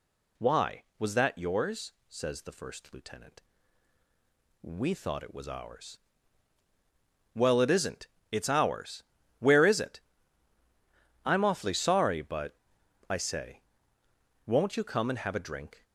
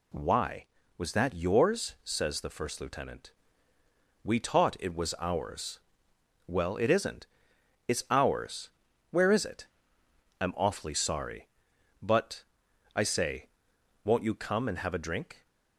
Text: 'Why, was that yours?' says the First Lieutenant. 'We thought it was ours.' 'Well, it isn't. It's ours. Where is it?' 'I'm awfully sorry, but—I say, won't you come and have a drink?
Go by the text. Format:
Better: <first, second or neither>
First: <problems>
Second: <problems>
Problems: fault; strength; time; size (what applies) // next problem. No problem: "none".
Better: first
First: none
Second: says "taught" for "thought"; at 4.4 s